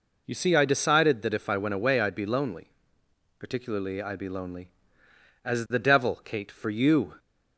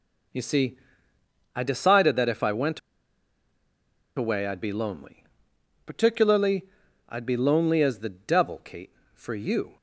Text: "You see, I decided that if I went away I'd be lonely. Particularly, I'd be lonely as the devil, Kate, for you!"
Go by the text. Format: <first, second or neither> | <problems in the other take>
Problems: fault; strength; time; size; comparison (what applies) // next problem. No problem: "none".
first | pauses between "went" and "away"; strong; at 2.7 s; 1.3 s long